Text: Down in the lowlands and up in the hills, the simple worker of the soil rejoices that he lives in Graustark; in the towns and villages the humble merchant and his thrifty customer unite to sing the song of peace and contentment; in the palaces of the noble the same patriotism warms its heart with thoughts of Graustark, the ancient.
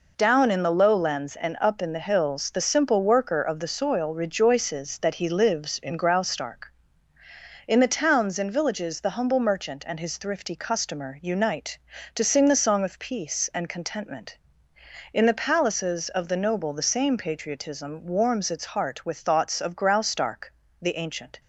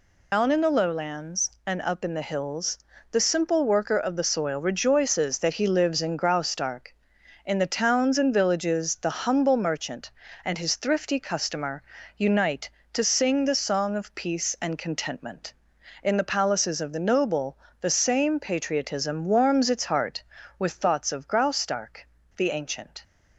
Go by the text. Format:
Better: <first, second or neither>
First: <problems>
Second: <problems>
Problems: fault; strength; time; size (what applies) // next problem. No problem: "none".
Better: first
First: none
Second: loses the start of "Down"; at 0.3 s; 150 ms // pauses between "customer" and "unite"; slight; at 11.8 s; 0.32 s long // pauses between "noble" and "the"; slight; at 17.5 s; 0.24 s long